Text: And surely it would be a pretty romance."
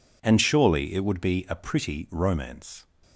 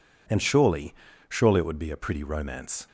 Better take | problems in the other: first | says "surely" twice; at 1.2 s

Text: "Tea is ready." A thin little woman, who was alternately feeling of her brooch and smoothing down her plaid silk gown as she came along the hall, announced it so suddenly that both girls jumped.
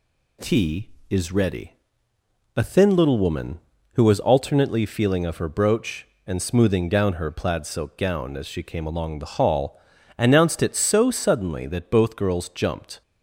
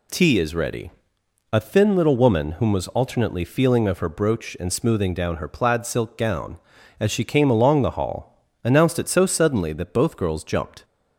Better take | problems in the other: first | says "whom" for "who"; at 2.5 s

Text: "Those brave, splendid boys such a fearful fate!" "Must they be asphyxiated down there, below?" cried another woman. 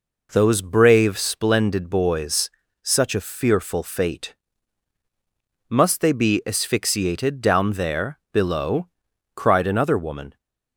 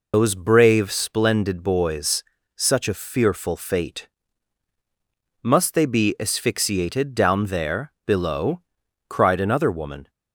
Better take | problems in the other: first | loses the start of "Those"; at 0.1 s; 90 ms // pauses between "boys" and "such"; slight; at 2.2 s; 0.32 s long; slight in the first

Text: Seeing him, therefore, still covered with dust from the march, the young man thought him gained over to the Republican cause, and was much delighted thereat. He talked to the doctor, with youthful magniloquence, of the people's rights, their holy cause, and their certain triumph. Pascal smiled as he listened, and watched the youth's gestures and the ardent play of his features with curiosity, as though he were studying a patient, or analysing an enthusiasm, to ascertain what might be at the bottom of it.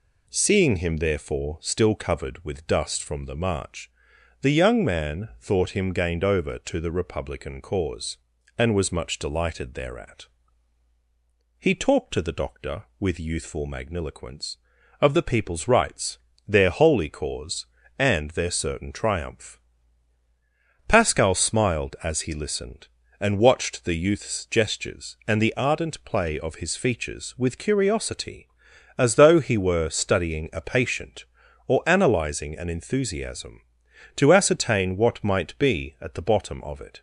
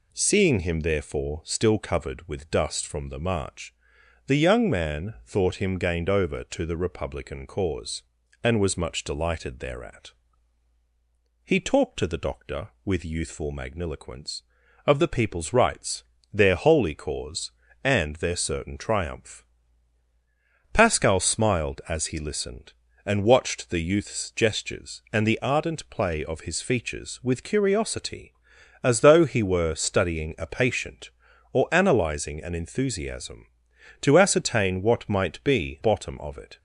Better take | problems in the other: first | skips "at the"; at 35.8 s

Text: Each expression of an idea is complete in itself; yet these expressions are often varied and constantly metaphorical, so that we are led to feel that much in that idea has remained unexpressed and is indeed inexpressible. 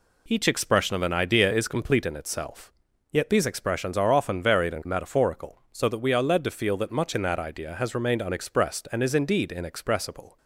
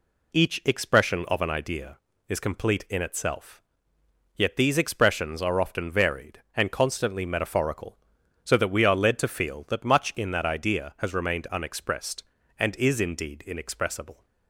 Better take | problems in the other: second | skips "constantly"; at 4.8 s

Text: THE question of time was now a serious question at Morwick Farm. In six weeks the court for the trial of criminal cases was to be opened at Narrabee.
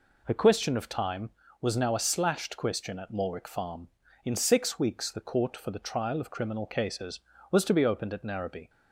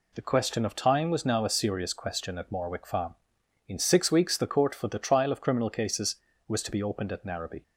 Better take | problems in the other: second | says "slashed" for "serious"; at 2.0 s

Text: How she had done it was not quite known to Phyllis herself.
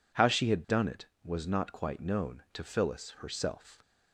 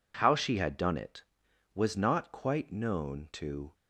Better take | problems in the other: first | stops before "Phyllis herself"; at 3.7 s

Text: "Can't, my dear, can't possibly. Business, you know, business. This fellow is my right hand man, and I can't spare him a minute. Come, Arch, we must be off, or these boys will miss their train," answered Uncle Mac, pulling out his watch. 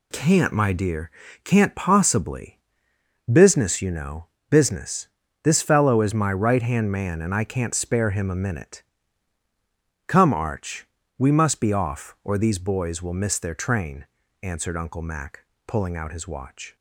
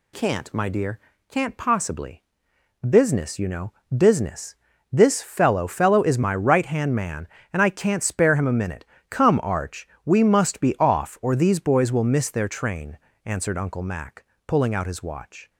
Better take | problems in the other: first | says "fellow" twice; at 5.6 s

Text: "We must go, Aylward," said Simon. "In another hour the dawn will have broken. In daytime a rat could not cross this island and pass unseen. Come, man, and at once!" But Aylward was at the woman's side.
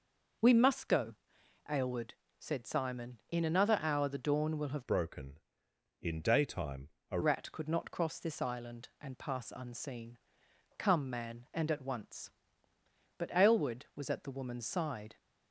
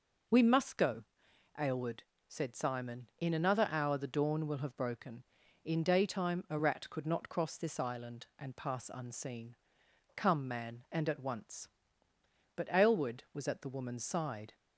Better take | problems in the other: second | changes voice from "broken" to "a"; from 4.8 to 7.1 s; 2.3 s long // pauses between "daytime" and "a"; slight; at 6.8 s; 0.22 s long

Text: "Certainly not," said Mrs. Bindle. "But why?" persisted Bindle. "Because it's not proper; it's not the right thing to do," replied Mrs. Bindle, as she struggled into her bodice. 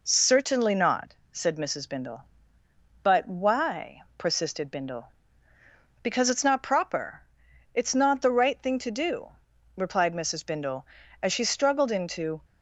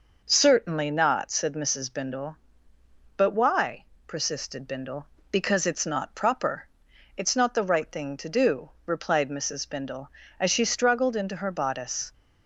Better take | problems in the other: second | stops before "her bodice"; at 12.4 s

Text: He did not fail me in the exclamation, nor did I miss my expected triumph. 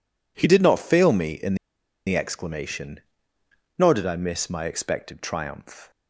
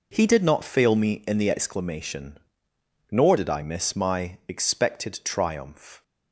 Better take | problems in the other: second | pauses between "in" and "the"; noticeable; at 1.5 s; 0.51 s long

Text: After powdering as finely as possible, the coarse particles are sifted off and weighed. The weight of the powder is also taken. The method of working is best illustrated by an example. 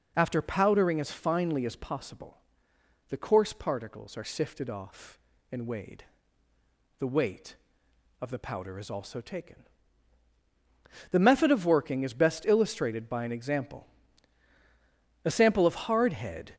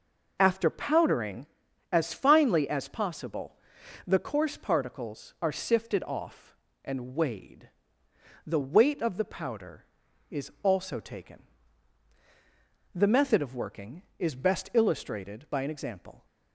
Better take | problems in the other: second | goes on to say "A sample of hardhead"; noticeable; from 15.2 s on; 1.3 s long

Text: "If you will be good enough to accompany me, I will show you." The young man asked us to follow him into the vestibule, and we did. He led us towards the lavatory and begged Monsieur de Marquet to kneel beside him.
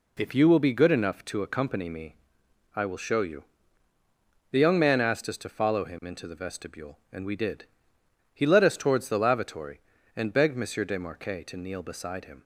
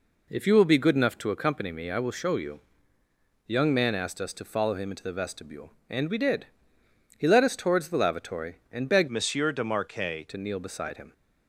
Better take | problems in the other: first | changes voice from "Monsieur" to "Marquet"; from 9.0 to 10.2 s; 1.2 s long

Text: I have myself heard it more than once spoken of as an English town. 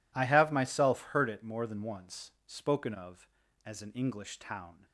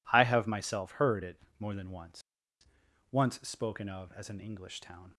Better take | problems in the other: first | pauses between "it" and "more"; slight; at 1.3 s; 0.22 s long // says "once" twice; at 3.0 s

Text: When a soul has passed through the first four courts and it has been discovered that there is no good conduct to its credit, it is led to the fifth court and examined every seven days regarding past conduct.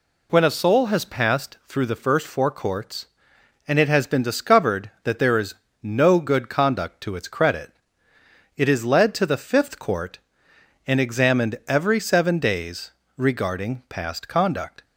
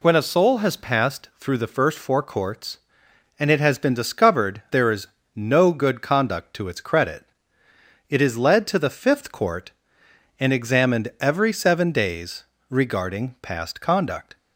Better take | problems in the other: first | skips "that"; at 4.6 s // pauses between "is" and "no"; slight; at 5.0 s; 0.26 s long; slight in the first // pauses between "days" and "regarding"; slight; at 12.4 s; 0.24 s long; slight in the first

